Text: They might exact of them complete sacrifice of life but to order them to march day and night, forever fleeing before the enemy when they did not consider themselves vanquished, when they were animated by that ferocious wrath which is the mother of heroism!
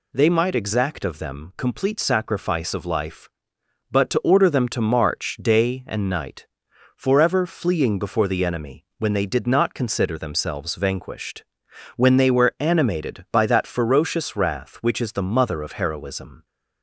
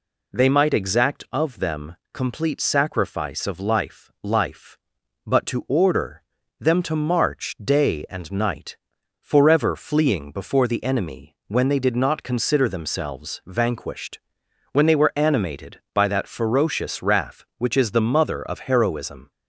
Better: first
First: none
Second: pauses between "them" and "complete"; slight; at 1.9 s; 0.16 s long // says "life" twice; at 4.2 s // pauses between "order" and "them"; slight; at 6.2 s; 0.36 s long

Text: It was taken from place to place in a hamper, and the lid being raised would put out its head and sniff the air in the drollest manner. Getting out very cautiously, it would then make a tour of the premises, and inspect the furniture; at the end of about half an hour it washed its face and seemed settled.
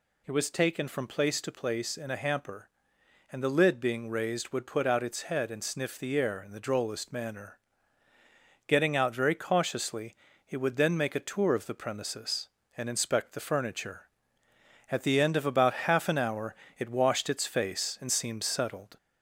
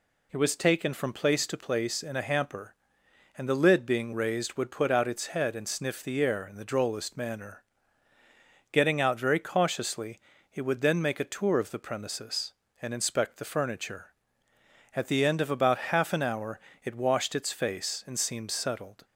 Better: second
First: gets louder; slight; throughout; 2.5 dB // pauses between "hour" and "it"; slight; at 16.5 s; 0.22 s long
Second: pauses between "hour" and "it"; slight; at 16.6 s; 0.24 s long

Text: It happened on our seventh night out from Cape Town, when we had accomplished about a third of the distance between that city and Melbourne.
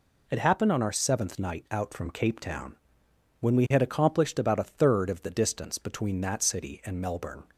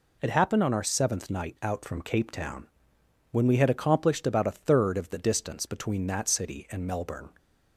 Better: neither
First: none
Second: none

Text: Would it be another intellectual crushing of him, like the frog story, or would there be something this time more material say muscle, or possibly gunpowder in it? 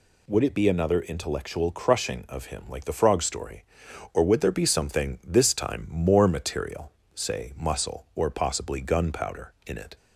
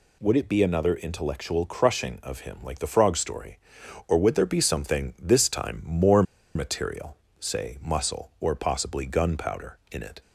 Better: first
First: pauses between "material" and "say"; slight; at 6.9 s; 0.24 s long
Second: pauses between "more" and "material"; slight; at 6.2 s; 0.32 s long // pauses between "material" and "say"; slight; at 7.1 s; 0.24 s long

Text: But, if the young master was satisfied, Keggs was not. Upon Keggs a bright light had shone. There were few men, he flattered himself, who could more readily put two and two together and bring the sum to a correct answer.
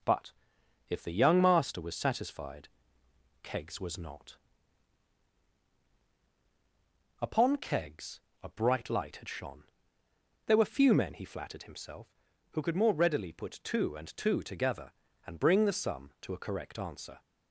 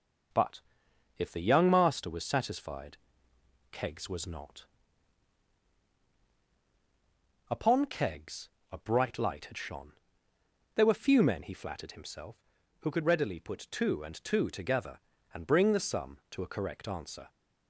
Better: first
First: pauses between "Keggs" and "a"; slight; at 8.2 s; 0.22 s long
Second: pauses between "Keggs" and "a"; slight; at 8.4 s; 0.22 s long // skips "more"; at 13.0 s

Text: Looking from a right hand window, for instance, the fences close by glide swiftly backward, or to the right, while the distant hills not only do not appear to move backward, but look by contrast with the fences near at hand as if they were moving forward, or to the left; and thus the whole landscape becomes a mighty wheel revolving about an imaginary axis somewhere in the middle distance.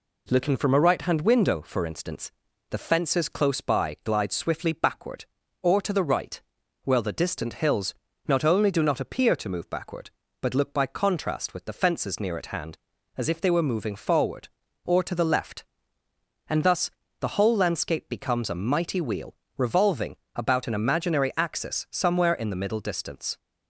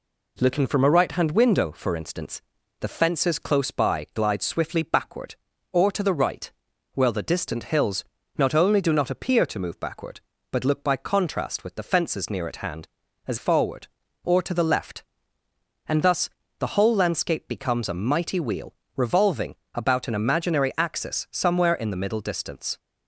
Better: first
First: pauses between "hills" and "not"; slight; at 7.9 s; 0.34 s long // pauses between "thus" and "the"; slight; at 16.9 s; 0.30 s long // pauses between "wheel" and "revolving"; slight; at 19.3 s; 0.22 s long // pauses between "revolving" and "about"; slight; at 20.1 s; 0.18 s long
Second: pauses between "hills" and "not"; slight; at 8.0 s; 0.34 s long // skips "if they were moving"; at 13.3 s // pauses between "thus" and "the"; slight; at 16.3 s; 0.30 s long // pauses between "wheel" and "revolving"; slight; at 18.7 s; 0.22 s long // pauses between "revolving" and "about"; slight; at 19.5 s; 0.18 s long

